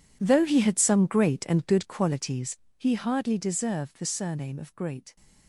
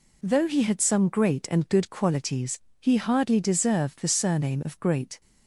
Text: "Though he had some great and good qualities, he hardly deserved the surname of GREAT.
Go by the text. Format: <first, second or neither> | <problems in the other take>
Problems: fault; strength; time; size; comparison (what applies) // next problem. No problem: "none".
second | gets quieter; strong; throughout; 17 dB